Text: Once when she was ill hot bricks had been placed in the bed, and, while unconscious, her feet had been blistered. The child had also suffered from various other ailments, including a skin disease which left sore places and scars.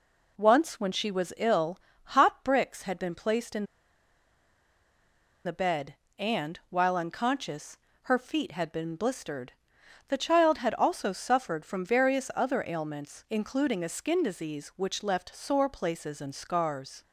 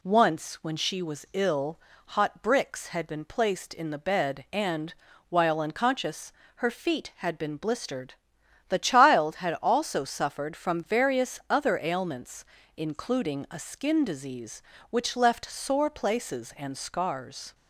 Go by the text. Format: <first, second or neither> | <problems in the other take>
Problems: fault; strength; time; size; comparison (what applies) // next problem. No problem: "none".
second | pauses between "ill" and "hot"; slight; at 1.7 s; 0.32 s long; also in the second // pauses between "in" and "the"; strong; at 3.6 s; 1.8 s long